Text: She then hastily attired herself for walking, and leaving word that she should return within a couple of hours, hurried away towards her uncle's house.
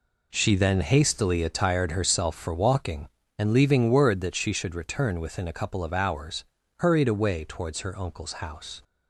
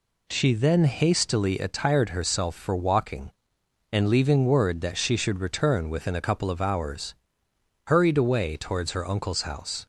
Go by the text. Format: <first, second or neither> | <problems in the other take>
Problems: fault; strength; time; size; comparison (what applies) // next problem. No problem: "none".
neither | none